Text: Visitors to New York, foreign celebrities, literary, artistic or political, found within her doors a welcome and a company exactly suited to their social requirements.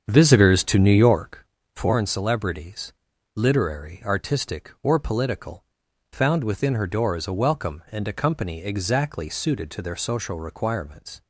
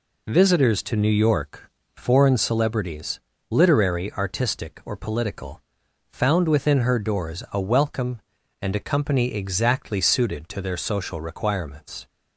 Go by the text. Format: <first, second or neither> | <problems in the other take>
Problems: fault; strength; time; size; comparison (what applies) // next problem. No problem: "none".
second | starts louder than the rest; strong; until 1.4 s; 7.5 dB